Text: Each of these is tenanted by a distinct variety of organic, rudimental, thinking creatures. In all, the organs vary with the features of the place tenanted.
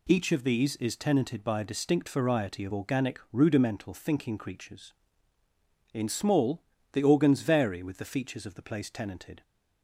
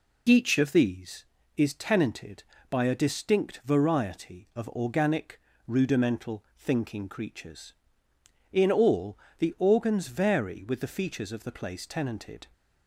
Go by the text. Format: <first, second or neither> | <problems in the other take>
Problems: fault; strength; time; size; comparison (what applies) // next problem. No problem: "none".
second | says "small" for "all"; at 6.0 s